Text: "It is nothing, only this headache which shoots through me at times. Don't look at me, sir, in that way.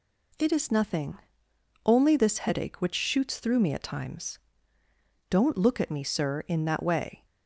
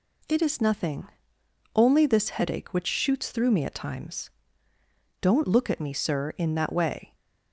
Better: neither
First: none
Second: none

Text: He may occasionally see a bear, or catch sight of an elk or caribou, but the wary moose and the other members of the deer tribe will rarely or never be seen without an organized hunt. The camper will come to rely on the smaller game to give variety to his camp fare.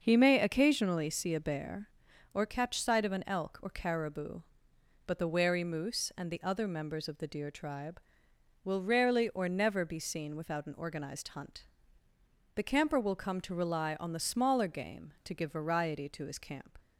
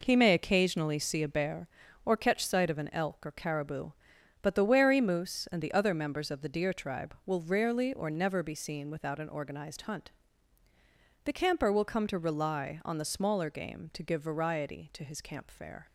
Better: second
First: starts louder than the rest; noticeable; until 1.0 s; 6 dB // stops before "fare"; at 16.7 s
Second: none

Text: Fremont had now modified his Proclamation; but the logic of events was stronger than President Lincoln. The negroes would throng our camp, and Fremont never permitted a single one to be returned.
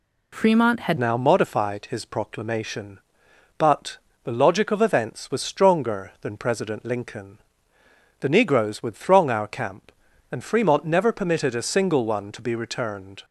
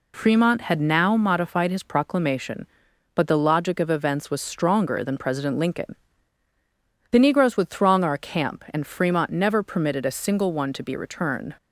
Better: second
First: changes voice at "now"; from 0.9 s on; 12.3 s long // pauses between "but" and "the"; slight; at 3.9 s; 0.26 s long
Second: none

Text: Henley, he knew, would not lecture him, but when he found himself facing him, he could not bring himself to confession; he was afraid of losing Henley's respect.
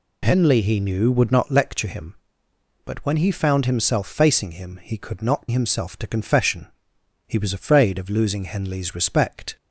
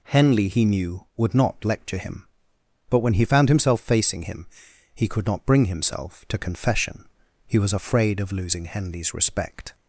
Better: second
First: skips "bring"; at 5.4 s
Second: none

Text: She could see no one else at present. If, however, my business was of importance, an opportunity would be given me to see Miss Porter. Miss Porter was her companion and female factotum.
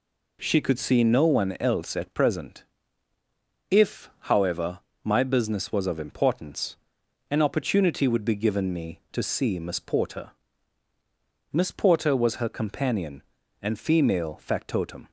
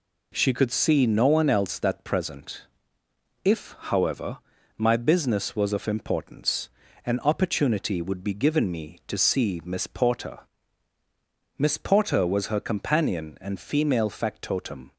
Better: first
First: none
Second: says "that" for "at"; at 1.7 s

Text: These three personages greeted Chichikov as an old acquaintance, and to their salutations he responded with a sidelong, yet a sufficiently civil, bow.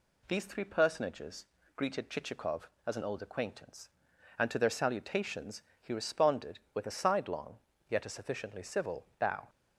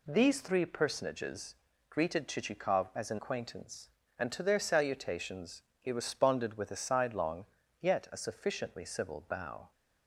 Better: first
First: pauses between "personages" and "greeted"; slight; at 1.4 s; 0.30 s long // pauses between "salutations" and "he"; slight; at 5.6 s; 0.20 s long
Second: pauses between "personages" and "greeted"; slight; at 1.5 s; 0.32 s long // skips "old"; at 3.1 s // pauses between "salutations" and "he"; slight; at 5.6 s; 0.18 s long

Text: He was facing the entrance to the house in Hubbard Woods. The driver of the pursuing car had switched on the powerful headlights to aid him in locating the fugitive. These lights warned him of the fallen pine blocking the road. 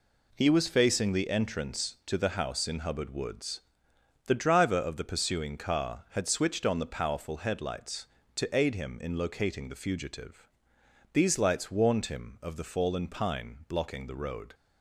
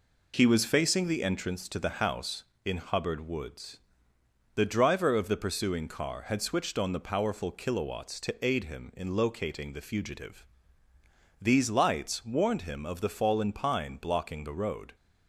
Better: first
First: none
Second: says "kilowatts" for "headlights"; at 7.5 s

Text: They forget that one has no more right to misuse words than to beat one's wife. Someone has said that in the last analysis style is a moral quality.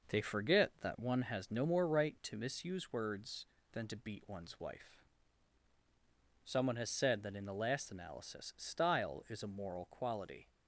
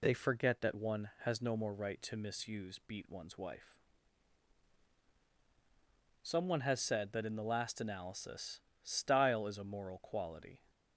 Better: first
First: none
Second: skips "words than to"; at 2.8 s // pauses between "analysis" and "style"; slight; at 8.6 s; 0.20 s long

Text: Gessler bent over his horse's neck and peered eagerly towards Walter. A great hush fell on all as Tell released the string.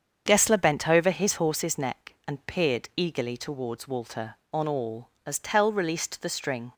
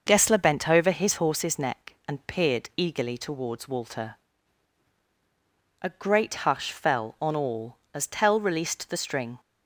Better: second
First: starts louder than the rest; strong; until 1.2 s; 7.5 dB // skips "A great hush fell"; at 4.4 s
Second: starts louder than the rest; noticeable; until 1.0 s; 6 dB

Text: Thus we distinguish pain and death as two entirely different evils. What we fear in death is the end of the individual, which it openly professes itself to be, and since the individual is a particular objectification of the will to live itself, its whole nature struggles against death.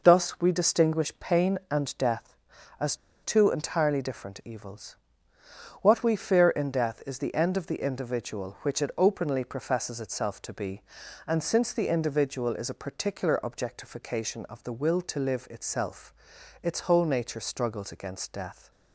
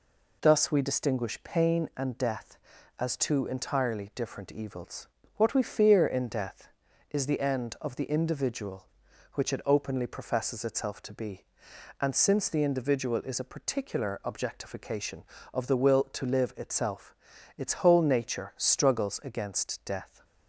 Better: second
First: pauses between "as" and "two"; slight; at 2.9 s; 0.27 s long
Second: none

